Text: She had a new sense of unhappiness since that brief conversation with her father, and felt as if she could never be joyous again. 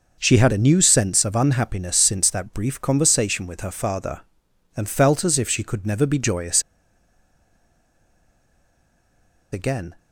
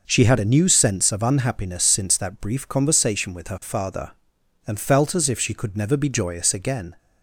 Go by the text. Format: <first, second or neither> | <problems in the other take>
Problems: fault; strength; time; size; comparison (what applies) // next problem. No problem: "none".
second | pauses between "joyous" and "again"; strong; at 6.6 s; 2.9 s long